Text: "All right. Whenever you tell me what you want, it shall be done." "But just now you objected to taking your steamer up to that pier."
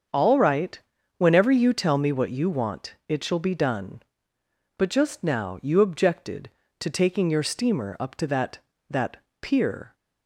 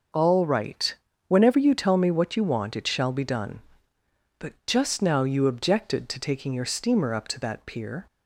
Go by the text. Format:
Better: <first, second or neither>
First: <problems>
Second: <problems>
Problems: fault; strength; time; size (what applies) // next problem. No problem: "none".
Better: second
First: starts louder than the rest; until 1.4 s; 6.5 dB // says "that" twice; at 8.8 s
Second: starts louder than the rest; noticeable; until 1.4 s; 6 dB